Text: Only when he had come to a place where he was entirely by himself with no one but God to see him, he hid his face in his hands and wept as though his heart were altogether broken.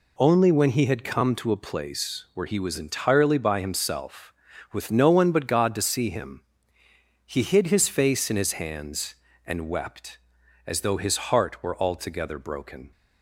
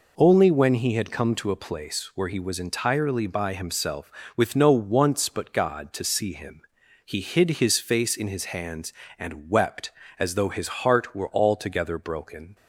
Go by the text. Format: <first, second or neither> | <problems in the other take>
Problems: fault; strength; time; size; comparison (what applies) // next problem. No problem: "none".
first | says "once" for "one"; at 4.7 s